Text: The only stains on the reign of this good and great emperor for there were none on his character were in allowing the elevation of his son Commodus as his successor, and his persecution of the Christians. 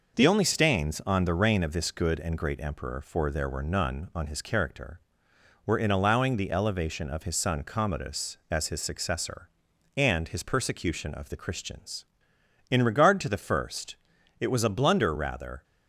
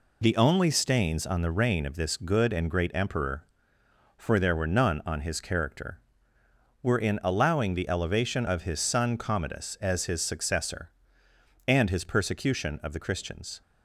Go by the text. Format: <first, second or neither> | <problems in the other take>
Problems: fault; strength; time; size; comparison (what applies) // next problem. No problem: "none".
second | goes on to say "In regard to the first it was a blunder rather"; strong; from 12.6 s on; 2.9 s long